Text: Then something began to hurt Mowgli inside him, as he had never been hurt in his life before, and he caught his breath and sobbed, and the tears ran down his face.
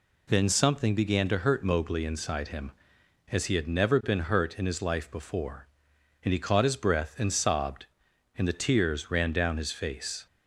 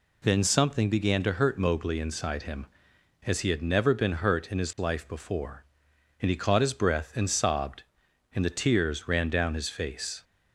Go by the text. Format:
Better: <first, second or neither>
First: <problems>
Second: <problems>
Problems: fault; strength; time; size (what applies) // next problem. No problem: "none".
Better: neither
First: none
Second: none